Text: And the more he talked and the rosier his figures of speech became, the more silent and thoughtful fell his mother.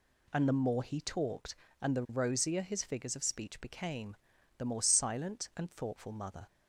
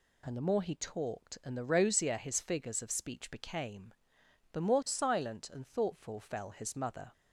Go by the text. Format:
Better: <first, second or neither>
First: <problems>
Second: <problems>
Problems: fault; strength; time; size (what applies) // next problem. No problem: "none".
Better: second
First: skips "fell his"; at 6.1 s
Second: none